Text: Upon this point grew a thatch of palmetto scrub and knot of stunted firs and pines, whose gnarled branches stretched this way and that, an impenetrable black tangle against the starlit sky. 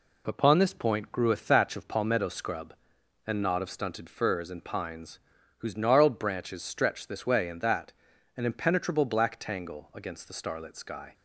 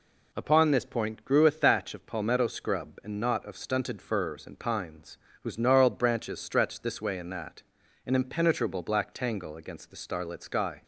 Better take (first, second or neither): neither